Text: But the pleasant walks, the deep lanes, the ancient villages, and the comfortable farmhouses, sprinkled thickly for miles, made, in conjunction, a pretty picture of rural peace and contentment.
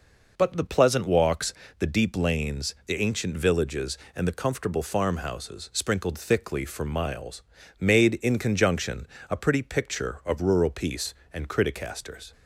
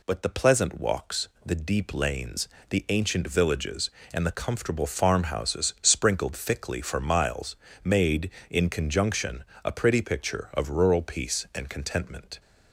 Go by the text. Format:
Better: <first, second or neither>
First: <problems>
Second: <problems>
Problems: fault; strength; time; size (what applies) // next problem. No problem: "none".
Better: second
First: says "criticasters" for "contentment"; at 11.4 s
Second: none